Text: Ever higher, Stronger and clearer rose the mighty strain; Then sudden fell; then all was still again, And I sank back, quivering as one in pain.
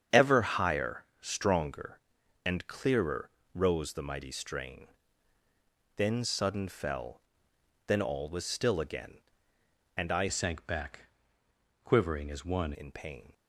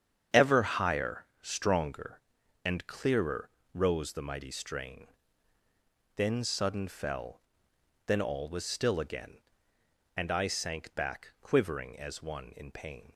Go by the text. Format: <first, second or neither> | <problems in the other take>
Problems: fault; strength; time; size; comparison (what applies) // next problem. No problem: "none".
second | starts louder than the rest; strong; until 1.2 s; 8 dB; strong in the second // pauses between "clearer" and "rose"; slight; at 3.2 s; 0.24 s long; slight in the second // changes voice from "sank" to "one"; from 10.2 to 12.7 s; 2.5 s long